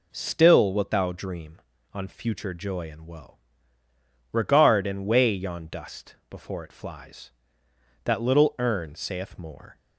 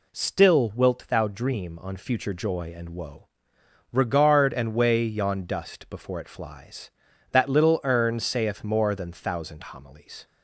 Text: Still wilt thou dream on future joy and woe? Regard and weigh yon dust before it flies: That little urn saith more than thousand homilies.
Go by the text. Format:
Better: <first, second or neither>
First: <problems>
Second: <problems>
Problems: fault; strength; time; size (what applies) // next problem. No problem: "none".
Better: second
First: stops before "than thousand homilies"; at 9.7 s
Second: none